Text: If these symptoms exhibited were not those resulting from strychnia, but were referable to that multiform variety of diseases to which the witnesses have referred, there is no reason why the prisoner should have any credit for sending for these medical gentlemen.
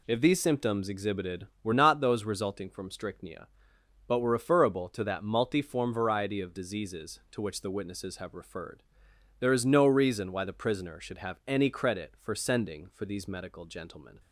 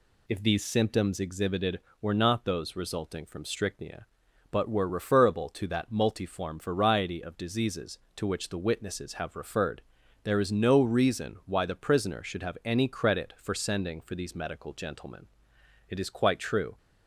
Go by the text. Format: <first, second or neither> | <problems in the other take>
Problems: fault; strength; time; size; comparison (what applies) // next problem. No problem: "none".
first | goes on to say "It is quite true"; noticeable; from 15.8 s on; 0.88 s long